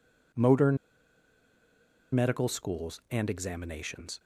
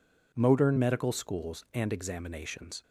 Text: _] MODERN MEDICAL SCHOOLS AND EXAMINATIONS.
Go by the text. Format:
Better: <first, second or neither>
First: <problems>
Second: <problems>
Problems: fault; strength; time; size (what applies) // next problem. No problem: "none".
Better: second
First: pauses between "MODERN" and "MEDICAL"; strong; at 0.7 s; 1.3 s long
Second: none